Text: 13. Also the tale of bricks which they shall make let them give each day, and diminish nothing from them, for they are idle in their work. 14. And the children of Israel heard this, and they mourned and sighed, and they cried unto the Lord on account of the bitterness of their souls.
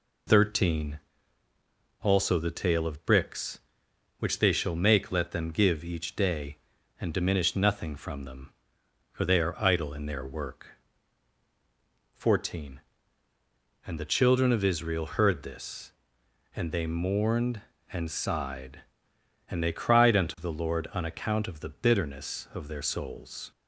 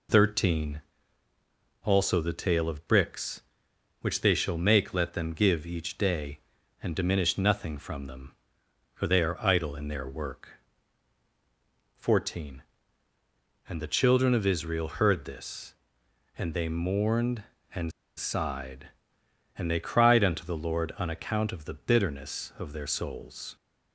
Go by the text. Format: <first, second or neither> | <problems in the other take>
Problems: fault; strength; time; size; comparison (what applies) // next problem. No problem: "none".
first | pauses between "and" and "sighed"; slight; at 17.9 s; 0.26 s long